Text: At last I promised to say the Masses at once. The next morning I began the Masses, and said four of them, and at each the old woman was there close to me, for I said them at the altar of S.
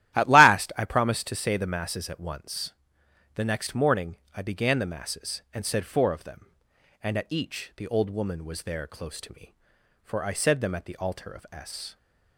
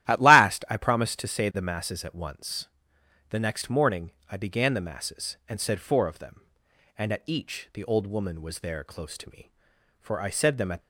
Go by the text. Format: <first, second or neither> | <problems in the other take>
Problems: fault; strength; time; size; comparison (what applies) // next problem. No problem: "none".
first | starts louder than the rest; strong; until 1.1 s; 13.5 dB; strong in the first // pauses between "morning" and "I"; slight; at 4.1 s; 0.18 s long; slight in the first // stops before "the altar of S"; at 10.8 s